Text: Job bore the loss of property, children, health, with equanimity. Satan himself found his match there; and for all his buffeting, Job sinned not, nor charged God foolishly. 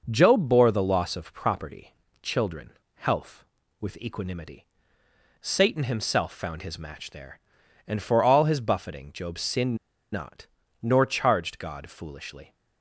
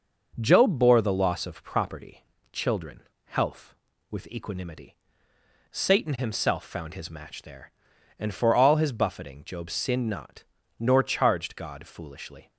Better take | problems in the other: second | starts louder than the rest; noticeable; until 1.1 s; 6 dB // pauses between "sinned" and "not"; slight; at 9.7 s; 0.35 s long

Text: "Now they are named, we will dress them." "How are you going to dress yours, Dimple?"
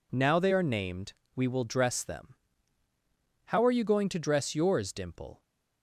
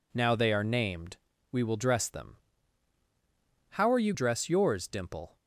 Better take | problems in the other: first | skips "going to"; at 4.1 s

